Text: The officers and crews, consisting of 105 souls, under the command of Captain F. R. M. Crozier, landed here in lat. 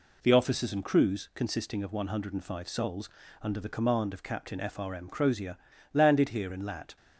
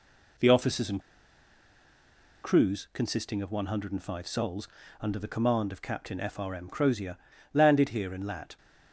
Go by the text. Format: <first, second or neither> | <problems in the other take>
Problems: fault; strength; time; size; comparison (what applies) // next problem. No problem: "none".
first | pauses between "and" and "crews"; strong; at 1.0 s; 1.4 s long